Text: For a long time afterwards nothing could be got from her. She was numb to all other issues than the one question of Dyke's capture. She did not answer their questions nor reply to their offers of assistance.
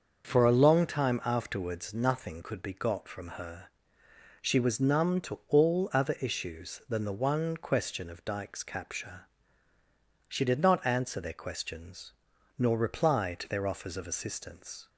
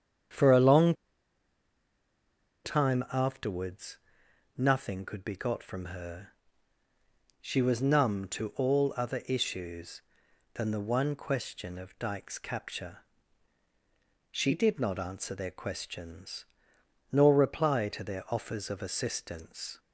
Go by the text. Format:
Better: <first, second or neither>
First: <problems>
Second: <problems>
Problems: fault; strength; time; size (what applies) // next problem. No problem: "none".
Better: first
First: starts louder than the rest; until 1.2 s; 6.5 dB // pauses between "questions" and "nor"; noticeable; at 12.1 s; 0.46 s long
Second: starts louder than the rest; strong; until 3.0 s; 8.5 dB // pauses between "long" and "time"; strong; at 0.9 s; 1.7 s long // pauses between "afterwards" and "nothing"; noticeable; at 3.9 s; 0.58 s long // pauses between "questions" and "nor"; noticeable; at 16.4 s; 0.66 s long